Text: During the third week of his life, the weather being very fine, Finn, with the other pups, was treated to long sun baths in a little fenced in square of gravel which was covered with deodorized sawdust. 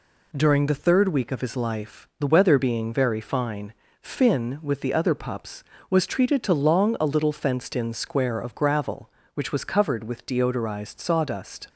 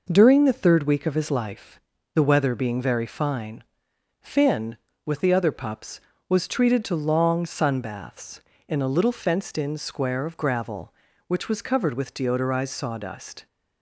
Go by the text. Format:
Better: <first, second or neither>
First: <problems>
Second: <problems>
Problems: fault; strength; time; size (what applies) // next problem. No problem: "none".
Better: second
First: skips "sun baths in"; at 6.9 s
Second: none